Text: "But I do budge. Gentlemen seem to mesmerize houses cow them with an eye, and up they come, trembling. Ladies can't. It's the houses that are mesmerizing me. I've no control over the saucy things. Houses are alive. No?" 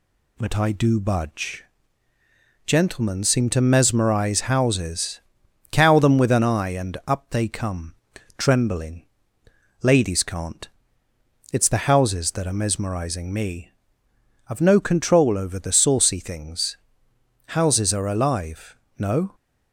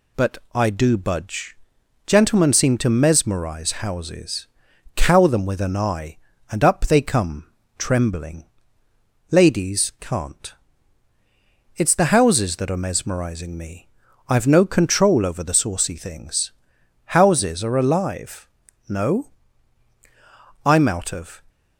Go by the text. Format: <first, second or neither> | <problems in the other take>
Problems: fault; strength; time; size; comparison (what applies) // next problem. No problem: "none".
first | pauses between "But" and "I"; slight; at 0.3 s; 0.16 s long // pauses between "houses" and "cow"; noticeable; at 4.4 s; 0.50 s long; noticeable in the first // goes on to say "I'm out of"; noticeable; from 20.6 s on; 0.76 s long